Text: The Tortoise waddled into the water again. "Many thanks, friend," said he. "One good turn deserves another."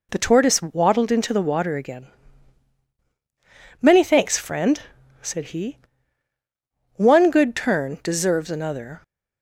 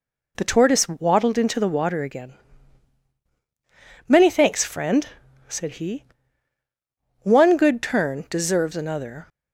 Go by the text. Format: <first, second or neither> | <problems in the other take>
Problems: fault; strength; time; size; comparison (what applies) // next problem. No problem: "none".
neither | none